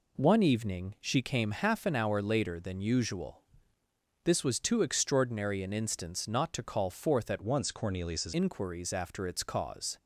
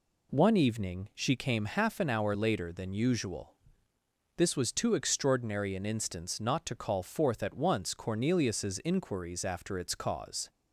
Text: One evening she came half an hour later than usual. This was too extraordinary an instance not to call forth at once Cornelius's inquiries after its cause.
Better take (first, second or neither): second